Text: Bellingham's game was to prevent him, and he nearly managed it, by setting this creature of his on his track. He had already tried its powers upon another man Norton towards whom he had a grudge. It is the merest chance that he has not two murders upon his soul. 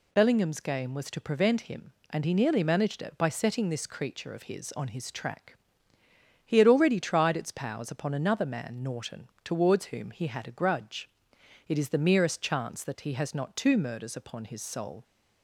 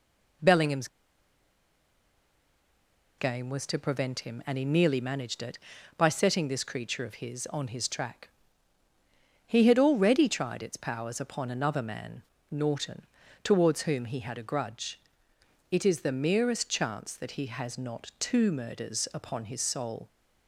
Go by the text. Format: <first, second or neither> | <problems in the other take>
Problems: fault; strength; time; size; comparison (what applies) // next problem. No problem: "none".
first | pauses between "Bellingham's" and "game"; strong; at 0.8 s; 2.3 s long // pauses between "man" and "Norton"; slight; at 12.2 s; 0.26 s long // pauses between "Norton" and "towards"; at 13.0 s; 0.38 s long; slight in the first